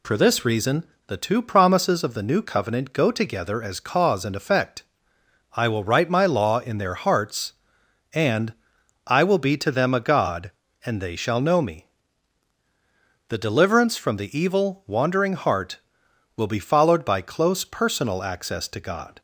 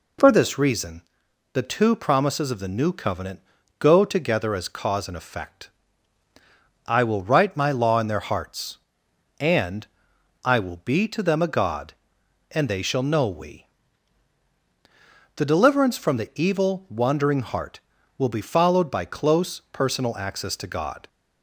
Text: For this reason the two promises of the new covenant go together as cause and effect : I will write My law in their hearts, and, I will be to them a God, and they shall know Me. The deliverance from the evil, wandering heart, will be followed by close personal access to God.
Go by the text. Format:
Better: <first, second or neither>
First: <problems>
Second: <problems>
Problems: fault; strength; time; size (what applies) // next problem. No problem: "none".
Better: first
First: pauses between "reason" and "the"; slight; at 0.8 s; 0.24 s long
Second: pauses between "reason" and "the"; noticeable; at 1.0 s; 0.52 s long // pauses between "covenant" and "go"; at 3.3 s; 0.40 s long // says "We" for "Me"; at 13.2 s